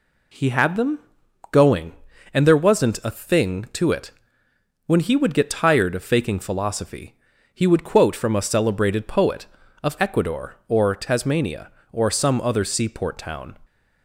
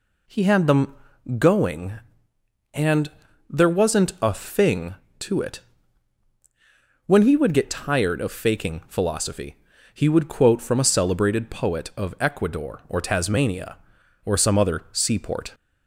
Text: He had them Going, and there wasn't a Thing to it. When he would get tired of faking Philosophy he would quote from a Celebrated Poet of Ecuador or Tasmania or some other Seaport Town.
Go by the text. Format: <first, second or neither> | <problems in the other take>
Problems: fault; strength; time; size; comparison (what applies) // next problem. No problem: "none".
first | pauses between "them" and "Going"; at 0.9 s; 0.42 s long; noticeable in the first // pauses between "and" and "there"; at 3.0 s; 0.38 s long // pauses between "Philosophy" and "he"; at 9.5 s; 0.40 s long; also in the first // stops before "Town"; at 15.5 s